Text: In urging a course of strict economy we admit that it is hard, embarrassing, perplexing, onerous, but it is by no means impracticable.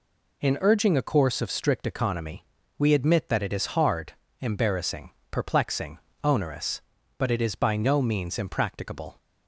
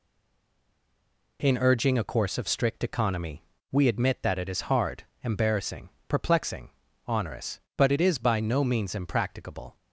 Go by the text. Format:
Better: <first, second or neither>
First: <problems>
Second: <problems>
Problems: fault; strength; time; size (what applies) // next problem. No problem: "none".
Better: first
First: pauses between "economy" and "we"; slight; at 2.4 s; 0.34 s long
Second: stays silent before the first word; noticeable; until 1.3 s; 1.3 s long // pauses between "economy" and "we"; slight; at 3.4 s; 0.30 s long